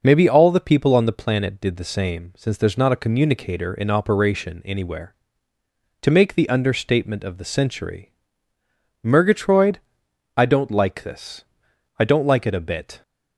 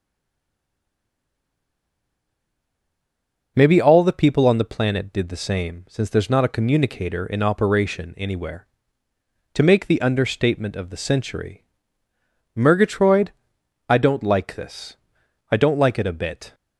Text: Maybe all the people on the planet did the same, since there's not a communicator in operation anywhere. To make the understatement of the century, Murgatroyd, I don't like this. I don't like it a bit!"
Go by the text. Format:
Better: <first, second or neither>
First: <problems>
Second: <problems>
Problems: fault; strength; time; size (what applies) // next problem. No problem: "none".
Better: first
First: none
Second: stays silent before the first word; strong; until 3.5 s; 3.5 s long